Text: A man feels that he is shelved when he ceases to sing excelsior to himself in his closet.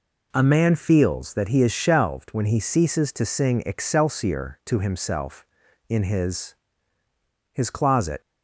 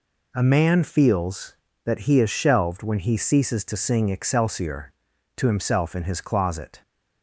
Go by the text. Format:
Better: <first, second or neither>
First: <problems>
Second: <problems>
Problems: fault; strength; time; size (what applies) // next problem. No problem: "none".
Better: second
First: says "his" twice; at 7.5 s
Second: none